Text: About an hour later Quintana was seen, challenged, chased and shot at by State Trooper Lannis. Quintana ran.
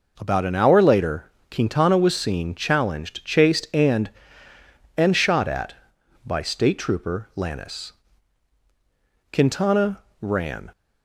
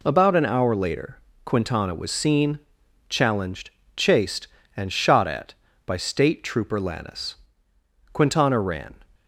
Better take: second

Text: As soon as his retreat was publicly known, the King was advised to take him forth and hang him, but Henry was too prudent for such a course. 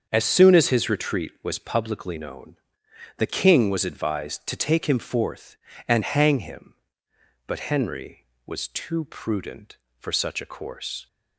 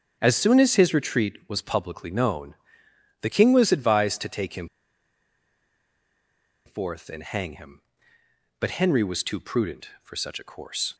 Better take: first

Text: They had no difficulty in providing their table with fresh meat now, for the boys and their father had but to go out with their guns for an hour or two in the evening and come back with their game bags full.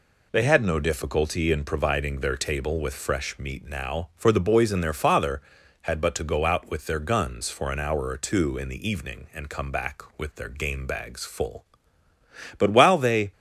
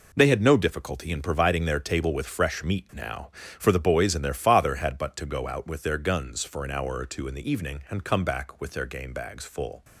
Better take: second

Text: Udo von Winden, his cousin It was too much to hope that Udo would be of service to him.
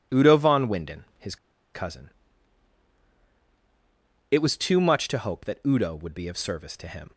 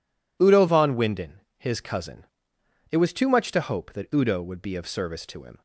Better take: second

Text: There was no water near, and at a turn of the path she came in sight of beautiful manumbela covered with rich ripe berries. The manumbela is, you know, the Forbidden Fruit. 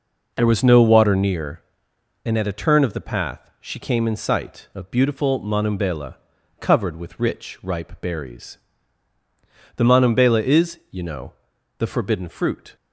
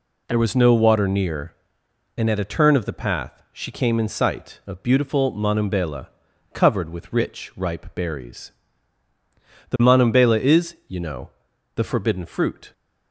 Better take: second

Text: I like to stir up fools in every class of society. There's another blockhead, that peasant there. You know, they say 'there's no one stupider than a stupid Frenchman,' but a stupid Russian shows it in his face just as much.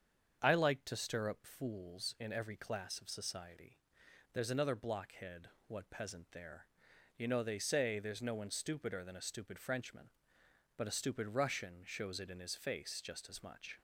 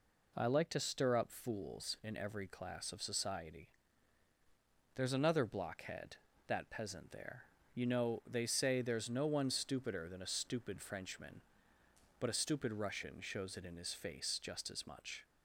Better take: second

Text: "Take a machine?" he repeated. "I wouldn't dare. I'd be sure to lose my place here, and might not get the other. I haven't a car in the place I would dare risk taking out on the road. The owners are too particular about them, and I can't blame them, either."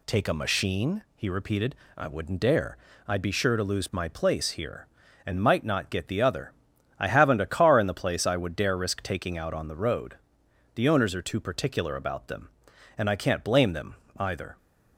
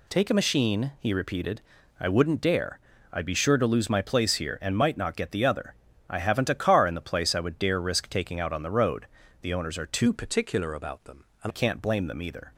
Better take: first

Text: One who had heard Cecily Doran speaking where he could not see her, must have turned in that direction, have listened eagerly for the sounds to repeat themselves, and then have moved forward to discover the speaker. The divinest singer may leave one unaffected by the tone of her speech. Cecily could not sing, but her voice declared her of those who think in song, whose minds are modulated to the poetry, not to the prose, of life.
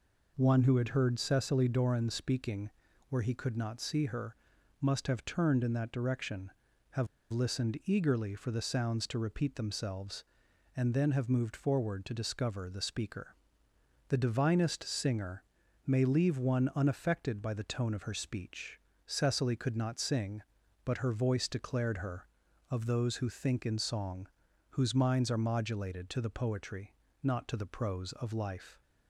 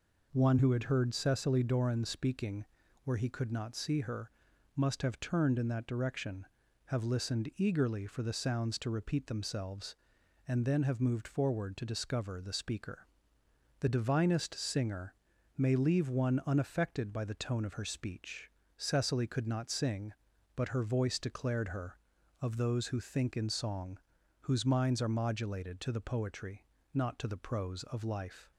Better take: second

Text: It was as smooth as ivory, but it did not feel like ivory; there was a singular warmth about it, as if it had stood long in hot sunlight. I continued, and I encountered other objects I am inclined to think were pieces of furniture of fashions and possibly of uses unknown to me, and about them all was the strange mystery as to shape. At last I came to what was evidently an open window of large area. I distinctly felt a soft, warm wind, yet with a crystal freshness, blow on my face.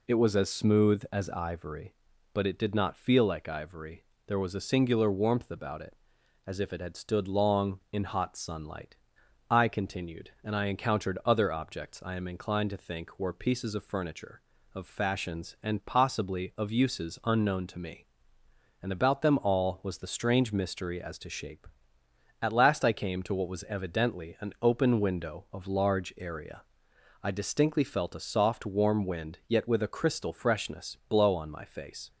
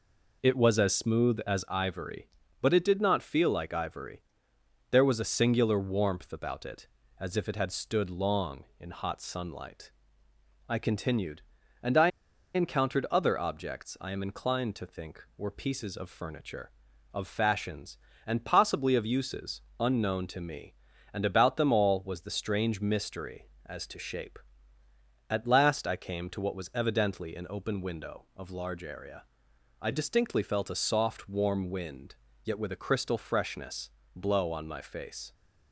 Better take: first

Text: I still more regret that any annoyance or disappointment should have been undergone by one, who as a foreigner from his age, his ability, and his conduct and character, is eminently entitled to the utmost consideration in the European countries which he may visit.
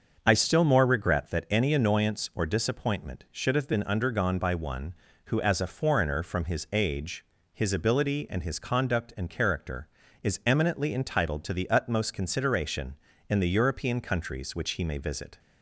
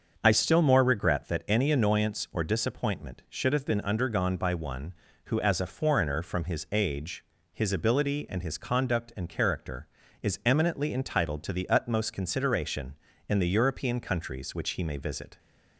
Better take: neither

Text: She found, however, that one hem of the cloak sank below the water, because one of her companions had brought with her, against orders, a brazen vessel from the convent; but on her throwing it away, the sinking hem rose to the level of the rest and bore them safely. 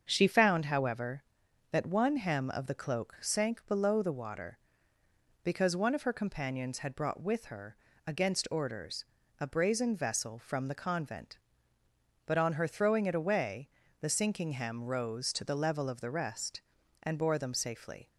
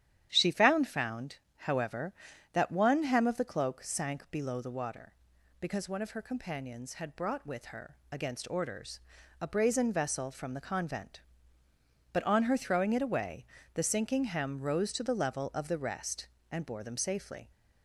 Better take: first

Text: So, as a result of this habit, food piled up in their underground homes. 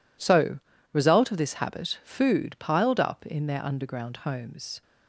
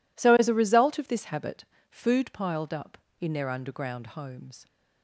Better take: second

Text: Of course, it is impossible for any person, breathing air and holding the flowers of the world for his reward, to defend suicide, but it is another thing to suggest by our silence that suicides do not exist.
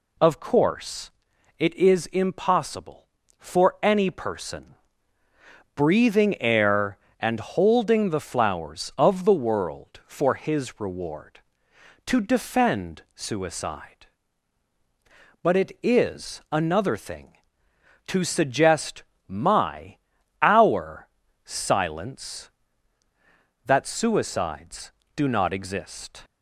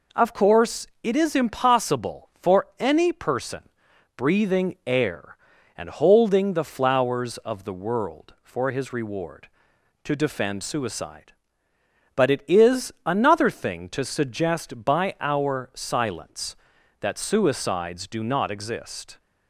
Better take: second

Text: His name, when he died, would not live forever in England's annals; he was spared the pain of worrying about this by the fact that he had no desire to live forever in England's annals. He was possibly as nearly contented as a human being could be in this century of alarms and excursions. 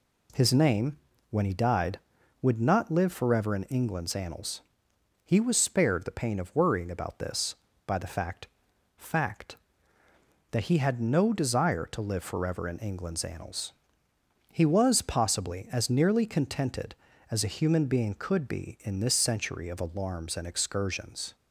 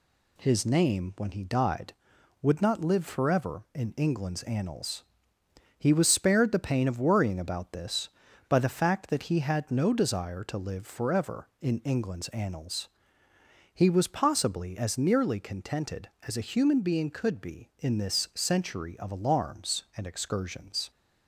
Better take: second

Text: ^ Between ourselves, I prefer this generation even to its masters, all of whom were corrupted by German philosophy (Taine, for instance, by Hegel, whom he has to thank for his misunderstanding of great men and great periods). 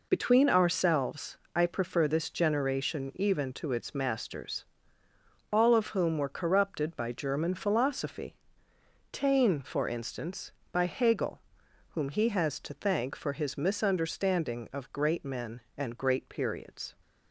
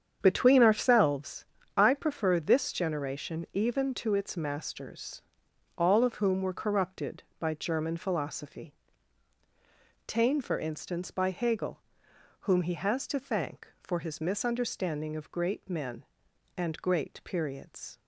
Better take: first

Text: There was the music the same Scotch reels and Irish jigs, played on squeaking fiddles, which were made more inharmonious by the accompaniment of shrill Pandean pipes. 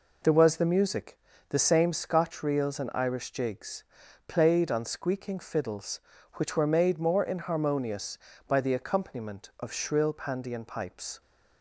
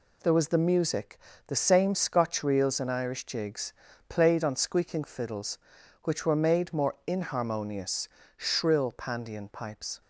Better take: first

